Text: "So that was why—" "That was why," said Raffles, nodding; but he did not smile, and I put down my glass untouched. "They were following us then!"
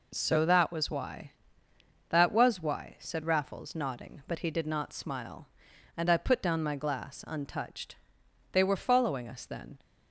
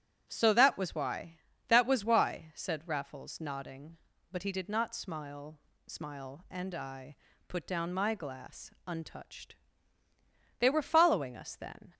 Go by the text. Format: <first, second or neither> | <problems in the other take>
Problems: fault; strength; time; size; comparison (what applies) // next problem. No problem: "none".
first | starts louder than the rest; strong; until 1.3 s; 9 dB // says "smile" twice; at 5.8 s // pauses between "I" and "put"; slight; at 7.1 s; 0.32 s long